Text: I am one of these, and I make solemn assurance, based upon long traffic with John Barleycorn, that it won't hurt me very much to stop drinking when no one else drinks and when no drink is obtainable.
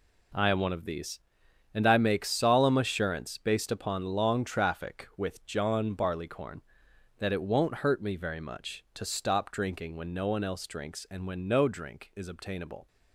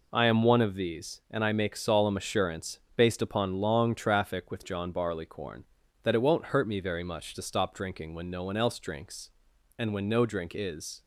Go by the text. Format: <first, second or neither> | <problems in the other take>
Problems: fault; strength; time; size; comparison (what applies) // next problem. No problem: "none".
first | stops before "obtainable"; at 11.0 s